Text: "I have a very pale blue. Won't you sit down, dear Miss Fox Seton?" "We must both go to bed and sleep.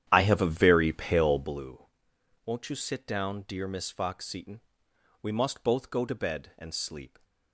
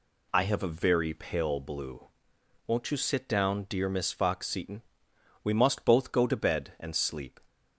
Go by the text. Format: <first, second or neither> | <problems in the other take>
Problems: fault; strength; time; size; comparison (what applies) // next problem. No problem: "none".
second | starts louder than the rest; strong; until 1.7 s; 10.5 dB